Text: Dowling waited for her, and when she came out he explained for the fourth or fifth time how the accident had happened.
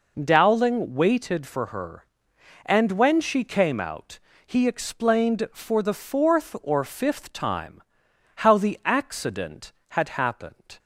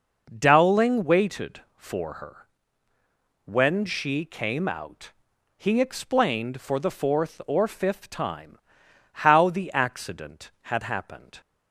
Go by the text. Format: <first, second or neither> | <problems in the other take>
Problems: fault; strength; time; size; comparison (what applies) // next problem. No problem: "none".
first | skips "and"; at 2.9 s // pauses between "out" and "he"; noticeable; at 5.1 s; 0.46 s long; slight in the first // pauses between "time" and "how"; noticeable; at 8.5 s; 0.54 s long; noticeable in the first